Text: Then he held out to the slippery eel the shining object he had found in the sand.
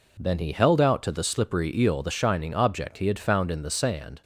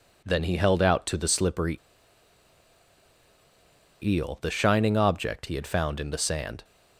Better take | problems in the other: first | pauses between "slippery" and "eel"; strong; at 1.7 s; 2.2 s long

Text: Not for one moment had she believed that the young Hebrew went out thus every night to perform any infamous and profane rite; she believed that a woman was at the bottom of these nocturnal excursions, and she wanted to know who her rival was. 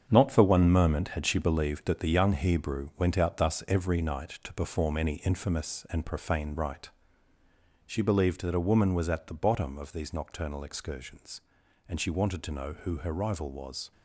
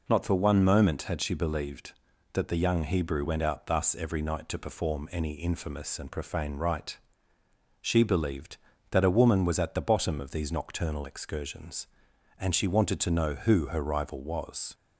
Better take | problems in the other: second | gets quieter; strong; throughout; 9 dB

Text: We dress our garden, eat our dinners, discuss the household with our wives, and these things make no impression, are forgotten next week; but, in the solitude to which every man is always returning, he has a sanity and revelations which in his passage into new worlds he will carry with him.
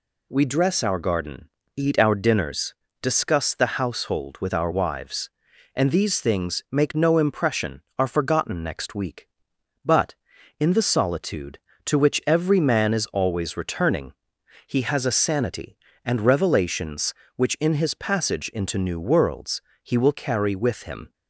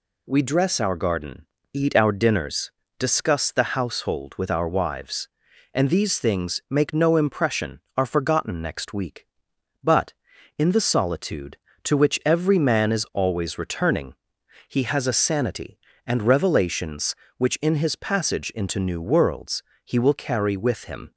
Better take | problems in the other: neither | pauses between "worlds" and "he"; slight; the same in both

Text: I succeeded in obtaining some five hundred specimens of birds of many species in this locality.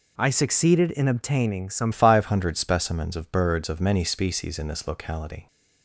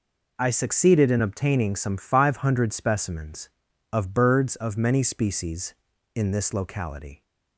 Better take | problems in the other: second | changes voice at "five"; from 1.9 s on; 3.5 s long

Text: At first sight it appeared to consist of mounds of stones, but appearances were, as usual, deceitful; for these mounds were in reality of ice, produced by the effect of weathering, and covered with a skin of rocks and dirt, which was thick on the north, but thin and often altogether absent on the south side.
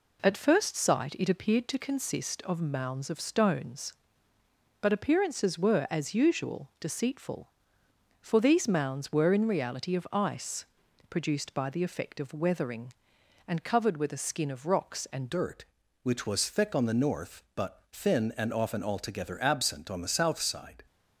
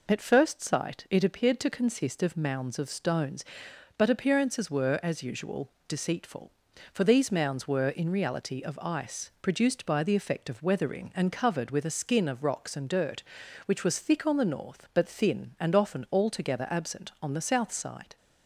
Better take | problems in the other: second | changes voice at "dirt"; from 15.2 s on; 5.6 s long

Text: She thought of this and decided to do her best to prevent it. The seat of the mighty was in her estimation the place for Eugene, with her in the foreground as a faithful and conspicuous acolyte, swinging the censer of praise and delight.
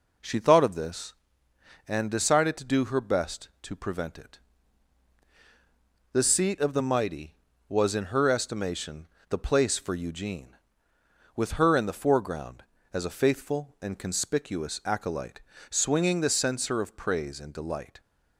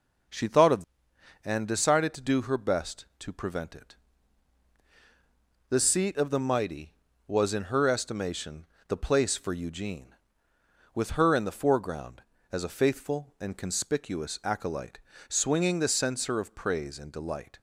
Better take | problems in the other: first | skips "this"; at 1.1 s // pauses between "estimation" and "the"; slight; at 8.6 s; 0.22 s long; slight in the first

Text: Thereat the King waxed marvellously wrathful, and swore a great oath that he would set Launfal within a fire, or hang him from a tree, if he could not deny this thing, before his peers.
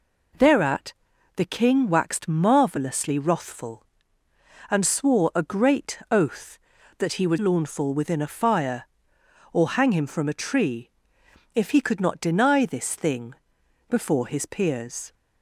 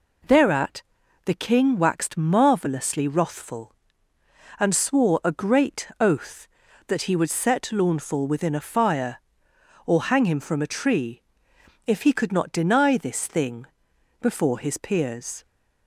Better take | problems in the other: second | pauses between "Thereat" and "the"; at 0.9 s; 0.42 s long; also in the second // skips "set"; at 7.3 s

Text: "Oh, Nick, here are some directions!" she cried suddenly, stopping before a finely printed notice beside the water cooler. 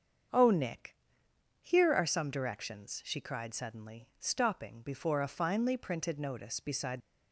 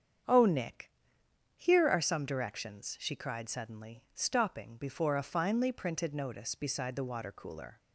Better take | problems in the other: second | starts louder than the rest; until 1.9 s; 7 dB; strong in the second // stops before "the water cooler"; at 7.0 s

